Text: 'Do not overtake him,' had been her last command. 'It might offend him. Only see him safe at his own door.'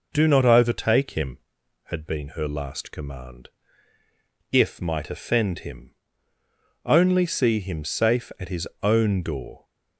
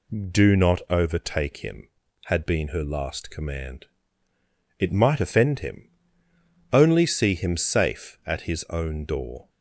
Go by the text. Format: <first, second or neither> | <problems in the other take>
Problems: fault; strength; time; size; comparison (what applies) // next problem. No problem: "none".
second | says "If" for "It"; at 4.5 s // pauses between "his" and "own"; slight; at 8.6 s; 0.16 s long